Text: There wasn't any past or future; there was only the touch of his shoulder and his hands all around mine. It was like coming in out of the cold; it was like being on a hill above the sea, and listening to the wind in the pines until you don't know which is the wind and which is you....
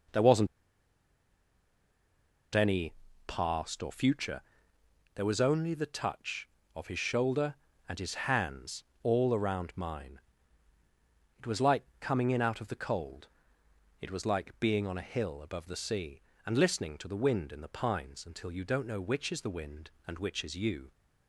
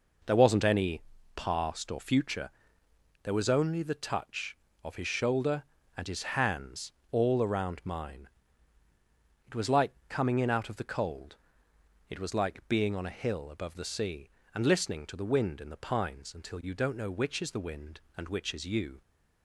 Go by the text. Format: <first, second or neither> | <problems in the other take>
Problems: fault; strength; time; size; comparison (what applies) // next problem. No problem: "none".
second | pauses between "wasn't" and "any"; strong; at 0.4 s; 2.0 s long // pauses between "any" and "past"; slight; at 2.9 s; 0.34 s long; slight in the second // pauses between "hands" and "all"; slight; at 8.8 s; 0.18 s long; slight in the second // pauses between "like" and "coming"; slight; at 11.8 s; 0.16 s long; slight in the second